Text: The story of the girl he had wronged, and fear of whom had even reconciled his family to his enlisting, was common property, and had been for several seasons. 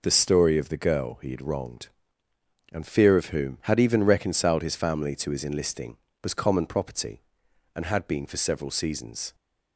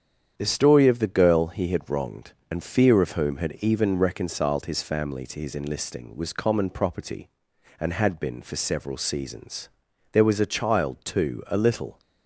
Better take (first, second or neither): first